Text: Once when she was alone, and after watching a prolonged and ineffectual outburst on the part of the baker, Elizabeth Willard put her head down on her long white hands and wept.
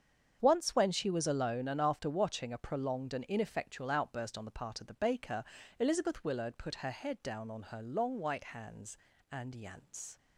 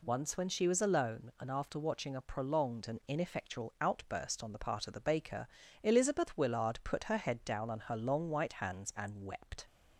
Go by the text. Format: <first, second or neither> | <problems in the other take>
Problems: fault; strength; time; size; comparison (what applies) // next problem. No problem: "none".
second | starts louder than the rest; strong; until 1.4 s; 7.5 dB // says "yance" for "wept"; at 9.5 s